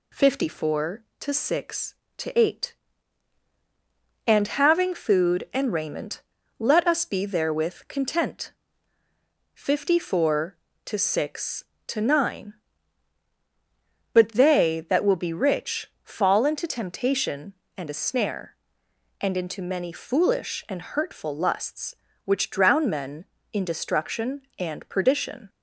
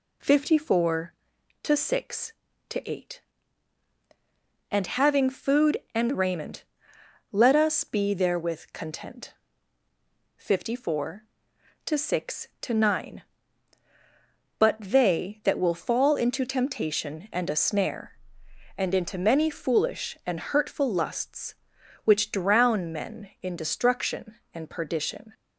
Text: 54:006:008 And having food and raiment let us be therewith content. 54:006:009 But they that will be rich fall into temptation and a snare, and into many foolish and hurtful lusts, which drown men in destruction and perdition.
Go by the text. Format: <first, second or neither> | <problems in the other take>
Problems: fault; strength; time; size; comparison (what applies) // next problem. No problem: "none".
first | pauses between "raiment" and "let"; noticeable; at 6.6 s; 0.68 s long; also in the first // skips "be rich"; at 15.7 s